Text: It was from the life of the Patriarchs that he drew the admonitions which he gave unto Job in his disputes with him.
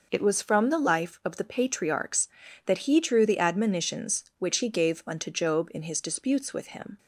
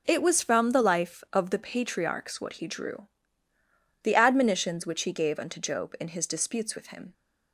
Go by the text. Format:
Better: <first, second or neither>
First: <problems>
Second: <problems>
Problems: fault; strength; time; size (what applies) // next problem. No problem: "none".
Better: first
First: none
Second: says "what" for "that"; at 2.4 s // pauses between "drew" and "the"; noticeable; at 3.0 s; 0.94 s long